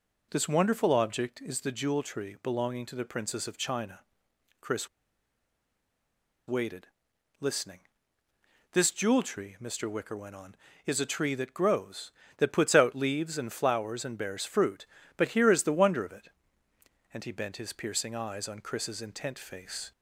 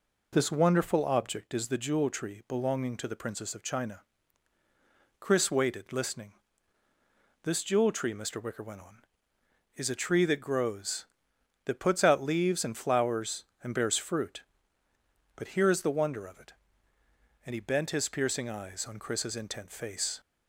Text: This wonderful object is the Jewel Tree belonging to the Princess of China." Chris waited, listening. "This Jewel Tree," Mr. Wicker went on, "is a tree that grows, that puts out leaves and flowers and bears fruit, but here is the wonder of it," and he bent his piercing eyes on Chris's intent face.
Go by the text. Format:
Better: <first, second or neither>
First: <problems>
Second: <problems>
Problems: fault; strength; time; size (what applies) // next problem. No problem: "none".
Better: second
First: pauses between "Chris" and "waited"; strong; at 4.8 s; 1.6 s long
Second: none